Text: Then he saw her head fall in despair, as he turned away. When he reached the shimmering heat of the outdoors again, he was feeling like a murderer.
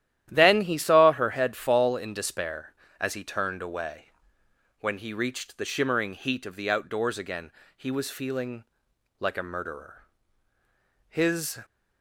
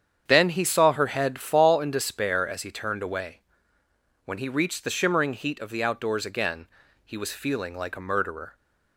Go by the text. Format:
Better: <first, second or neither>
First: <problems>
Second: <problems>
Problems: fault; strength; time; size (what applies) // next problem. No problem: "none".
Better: second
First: starts louder than the rest; strong; until 1.3 s; 12 dB // pauses between "feeling" and "like"; noticeable; at 8.6 s; 0.56 s long // goes on to say "His"; from 11.0 s on; 0.50 s long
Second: starts louder than the rest; strong; until 1.2 s; 8 dB